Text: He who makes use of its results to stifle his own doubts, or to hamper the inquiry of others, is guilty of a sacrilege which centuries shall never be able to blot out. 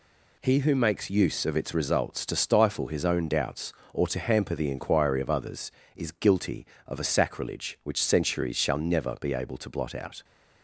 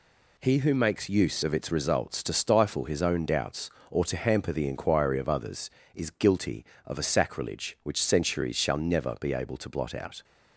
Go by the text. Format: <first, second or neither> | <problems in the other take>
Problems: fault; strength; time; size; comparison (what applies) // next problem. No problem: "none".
neither | none